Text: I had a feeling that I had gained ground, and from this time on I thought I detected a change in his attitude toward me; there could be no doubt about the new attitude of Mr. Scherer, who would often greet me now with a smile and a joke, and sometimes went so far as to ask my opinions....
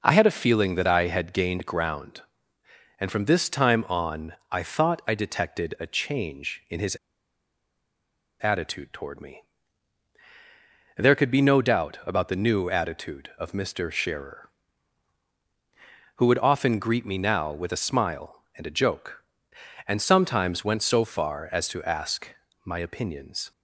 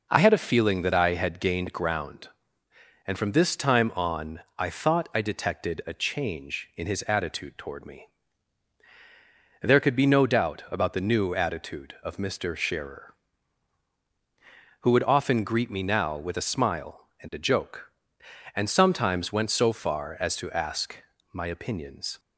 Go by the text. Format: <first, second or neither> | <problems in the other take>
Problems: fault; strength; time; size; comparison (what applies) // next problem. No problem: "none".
second | pauses between "on" and "I"; slight; at 4.3 s; 0.18 s long; slight in the second // pauses between "his" and "attitude"; strong; at 6.9 s; 1.4 s long // pauses between "ask" and "my"; slight; at 22.2 s; 0.34 s long; slight in the second